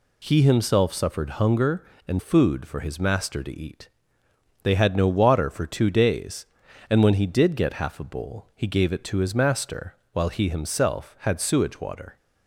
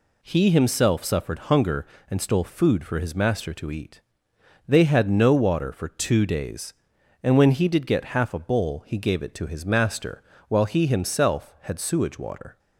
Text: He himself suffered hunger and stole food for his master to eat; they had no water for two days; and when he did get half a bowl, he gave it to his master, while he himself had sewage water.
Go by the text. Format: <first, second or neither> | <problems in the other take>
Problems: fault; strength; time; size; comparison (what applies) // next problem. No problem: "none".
second | skips "stole"; at 2.1 s